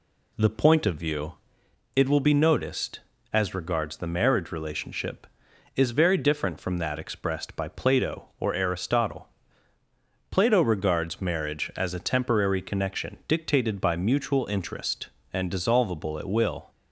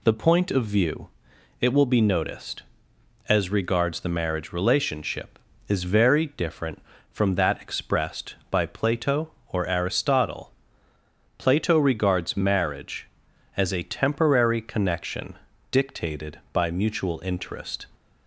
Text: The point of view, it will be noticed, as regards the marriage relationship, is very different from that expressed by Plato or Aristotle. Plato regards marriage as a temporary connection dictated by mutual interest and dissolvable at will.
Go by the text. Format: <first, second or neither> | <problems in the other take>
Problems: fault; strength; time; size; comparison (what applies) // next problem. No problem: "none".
first | pauses between "connection" and "dictated"; slight; at 15.3 s; 0.36 s long // stops before "and dissolvable at will"; at 17.9 s